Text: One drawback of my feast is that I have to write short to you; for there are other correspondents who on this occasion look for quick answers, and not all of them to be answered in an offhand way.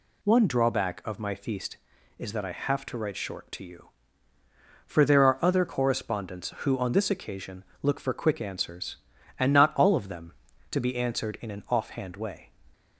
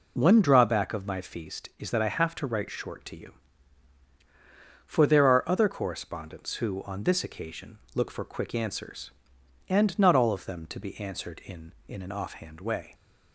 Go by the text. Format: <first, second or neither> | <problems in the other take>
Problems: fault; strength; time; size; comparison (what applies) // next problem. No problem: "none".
first | pauses between "occasion" and "look"; slight; at 7.7 s; 0.16 s long; slight in the first // says "in" twice; at 11.8 s